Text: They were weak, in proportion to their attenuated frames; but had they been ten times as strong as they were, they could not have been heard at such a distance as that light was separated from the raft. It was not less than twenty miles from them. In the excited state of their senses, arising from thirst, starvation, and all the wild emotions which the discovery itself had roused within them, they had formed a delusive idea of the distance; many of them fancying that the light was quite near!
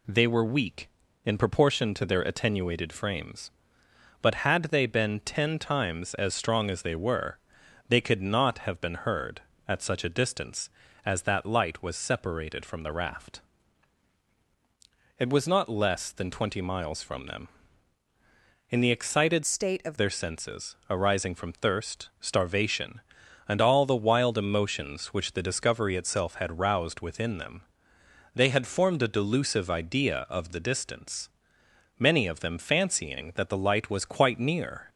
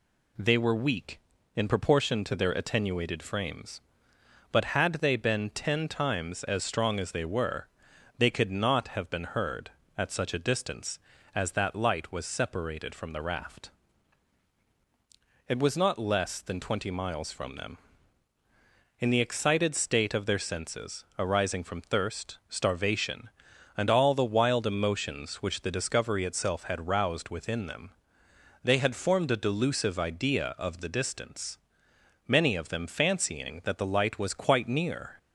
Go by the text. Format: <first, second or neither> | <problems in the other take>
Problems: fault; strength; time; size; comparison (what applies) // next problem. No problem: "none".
second | changes voice from "state" to "of"; from 19.4 to 19.9 s; 0.5 s long